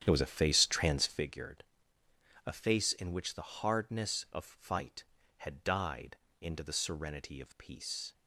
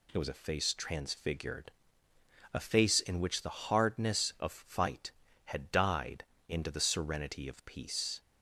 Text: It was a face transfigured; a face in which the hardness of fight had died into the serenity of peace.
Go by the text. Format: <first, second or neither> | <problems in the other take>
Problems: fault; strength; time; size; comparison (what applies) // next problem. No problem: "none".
second | starts louder than the rest; strong; until 1.3 s; 9.5 dB // pauses between "died" and "into"; slight; at 6.1 s; 0.24 s long; slight in the second